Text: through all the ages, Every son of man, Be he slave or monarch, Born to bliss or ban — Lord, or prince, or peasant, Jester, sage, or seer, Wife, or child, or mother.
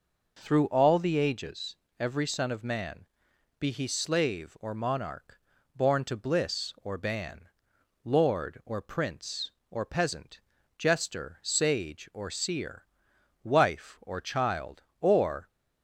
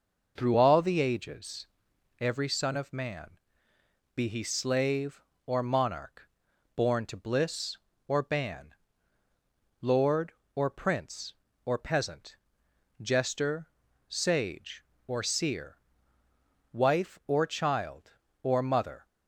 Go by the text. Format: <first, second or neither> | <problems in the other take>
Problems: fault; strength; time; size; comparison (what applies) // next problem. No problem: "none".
second | stops before "mother"; at 15.4 s